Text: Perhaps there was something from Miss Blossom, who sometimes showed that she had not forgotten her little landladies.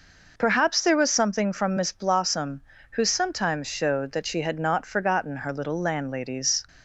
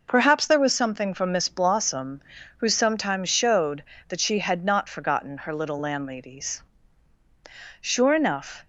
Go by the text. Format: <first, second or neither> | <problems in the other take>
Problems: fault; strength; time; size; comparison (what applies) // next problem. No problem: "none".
first | goes on to say "Sure enough"; noticeable; from 7.8 s on; 0.82 s long